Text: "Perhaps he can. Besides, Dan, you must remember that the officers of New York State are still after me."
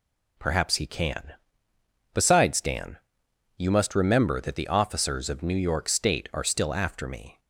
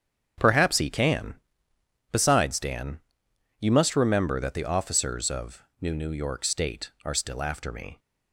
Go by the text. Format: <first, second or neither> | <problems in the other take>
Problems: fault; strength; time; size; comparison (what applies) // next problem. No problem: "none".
first | starts louder than the rest; strong; until 2.1 s; 8 dB // pauses between "of" and "New"; slight; at 5.6 s; 0.16 s long // says "New" twice; at 5.9 s